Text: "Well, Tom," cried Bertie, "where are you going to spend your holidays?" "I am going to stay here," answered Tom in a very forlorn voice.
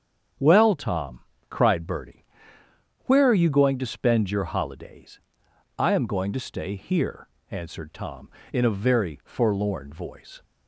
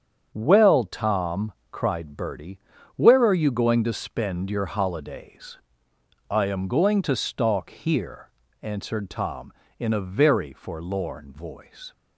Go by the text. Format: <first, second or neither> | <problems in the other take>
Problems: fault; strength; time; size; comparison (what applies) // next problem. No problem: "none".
first | starts louder than the rest; strong; until 1.3 s; 8 dB; strong in the first // says "stalk" for "stay"; at 7.1 s